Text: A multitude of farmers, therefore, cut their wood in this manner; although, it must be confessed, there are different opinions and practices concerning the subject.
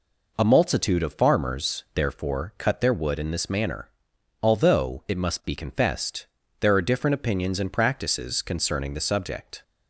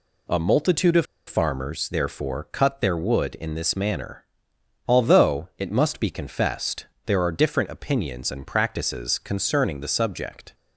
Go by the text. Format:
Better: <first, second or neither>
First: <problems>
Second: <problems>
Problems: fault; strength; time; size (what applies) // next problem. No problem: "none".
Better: first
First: none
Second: pauses between "of" and "farmers"; slight; at 1.0 s; 0.22 s long